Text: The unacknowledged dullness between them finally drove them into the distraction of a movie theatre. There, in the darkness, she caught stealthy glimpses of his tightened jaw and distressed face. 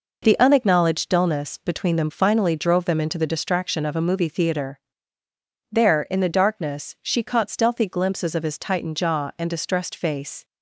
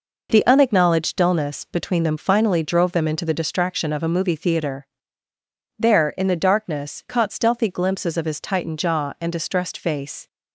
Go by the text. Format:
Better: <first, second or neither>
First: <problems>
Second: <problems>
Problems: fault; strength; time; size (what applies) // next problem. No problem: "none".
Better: first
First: none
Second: skips "she"; at 7.0 s